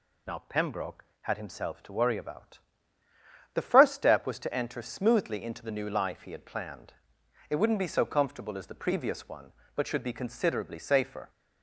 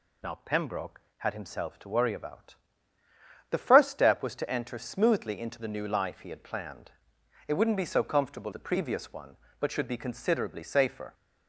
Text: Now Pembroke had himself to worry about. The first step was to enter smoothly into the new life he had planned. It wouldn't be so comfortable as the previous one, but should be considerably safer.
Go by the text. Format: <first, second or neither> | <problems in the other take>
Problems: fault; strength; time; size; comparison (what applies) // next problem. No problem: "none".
first | skips "as"; at 8.5 s